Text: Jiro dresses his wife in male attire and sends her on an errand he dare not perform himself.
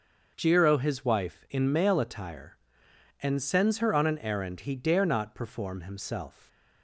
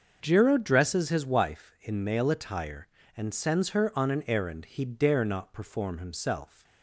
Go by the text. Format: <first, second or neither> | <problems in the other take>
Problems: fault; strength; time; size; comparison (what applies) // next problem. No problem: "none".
second | starts louder than the rest; until 1.3 s; 6 dB; also in the second // skips "dresses"; at 0.7 s